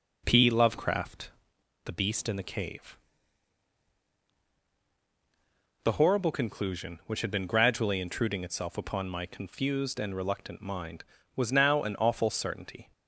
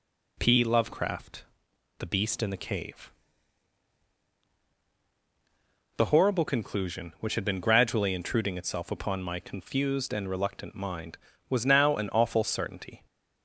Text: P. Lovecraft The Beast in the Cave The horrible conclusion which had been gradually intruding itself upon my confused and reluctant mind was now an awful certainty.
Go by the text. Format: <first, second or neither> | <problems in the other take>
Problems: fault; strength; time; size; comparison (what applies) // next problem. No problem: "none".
second | starts louder than the rest; noticeable; until 1.7 s; 4.5 dB // pauses between "Lovecraft" and "The"; noticeable; at 1.2 s; 0.56 s long; noticeable in the second // pauses between "Cave" and "The"; strong; at 2.9 s; 2.8 s long; strong in the second